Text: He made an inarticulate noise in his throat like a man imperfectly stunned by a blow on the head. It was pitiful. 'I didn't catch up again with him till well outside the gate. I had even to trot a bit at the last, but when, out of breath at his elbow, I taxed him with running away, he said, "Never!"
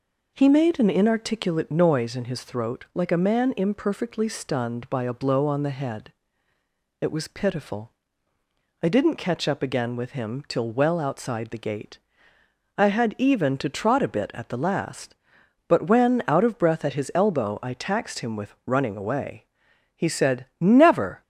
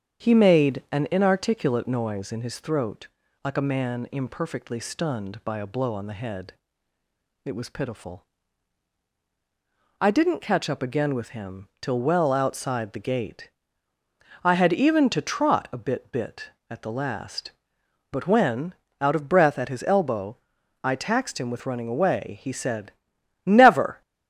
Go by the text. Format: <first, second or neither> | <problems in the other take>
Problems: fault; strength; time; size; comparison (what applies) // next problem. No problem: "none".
first | starts louder than the rest; strong; until 1.3 s; 8 dB // pauses between "throat" and "like"; slight; at 3.0 s; 0.36 s long // says "bit" twice; at 16.1 s